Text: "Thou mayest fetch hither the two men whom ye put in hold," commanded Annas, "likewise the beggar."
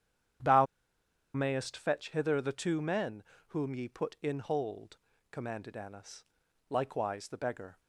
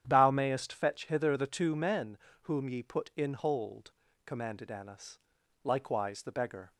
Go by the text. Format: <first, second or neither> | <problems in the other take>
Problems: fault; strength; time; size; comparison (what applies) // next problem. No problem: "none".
second | starts louder than the rest; strong; until 2.1 s; 9.5 dB; strong in the second // pauses between "Thou" and "mayest"; noticeable; at 0.6 s; 0.69 s long // pauses between "men" and "whom"; slight; at 3.2 s; 0.24 s long; slight in the second